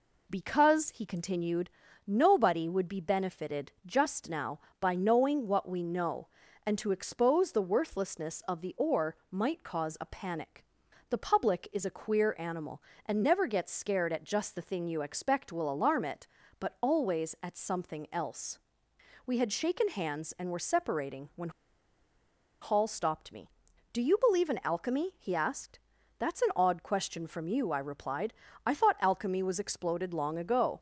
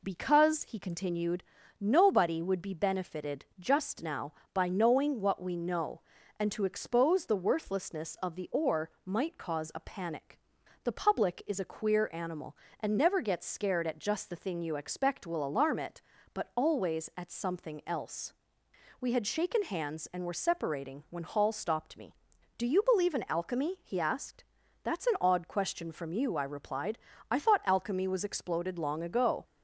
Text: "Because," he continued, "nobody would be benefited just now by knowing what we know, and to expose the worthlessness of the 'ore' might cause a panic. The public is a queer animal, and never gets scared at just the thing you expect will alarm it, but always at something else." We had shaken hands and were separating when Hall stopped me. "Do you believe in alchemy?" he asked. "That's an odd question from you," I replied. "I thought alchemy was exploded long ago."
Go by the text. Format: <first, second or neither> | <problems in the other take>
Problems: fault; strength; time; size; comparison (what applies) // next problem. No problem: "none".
second | pauses between "when" and "Hall"; at 21.4 s; 1.1 s long